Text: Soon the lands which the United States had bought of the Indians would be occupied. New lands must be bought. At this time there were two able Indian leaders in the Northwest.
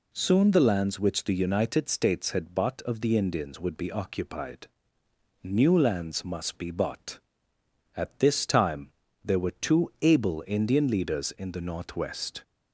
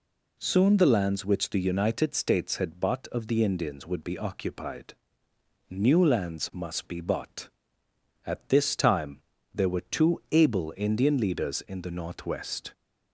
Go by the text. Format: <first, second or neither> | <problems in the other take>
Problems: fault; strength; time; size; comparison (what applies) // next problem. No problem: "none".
neither | pauses between "time" and "there"; slight; the same in both